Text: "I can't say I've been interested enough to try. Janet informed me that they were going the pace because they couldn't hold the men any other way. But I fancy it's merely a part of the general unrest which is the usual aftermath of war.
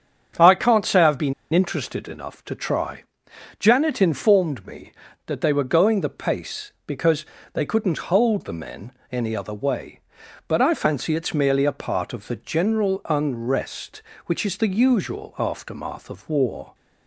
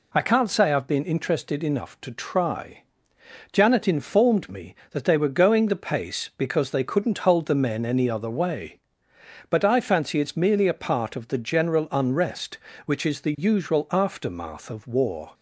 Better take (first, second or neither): second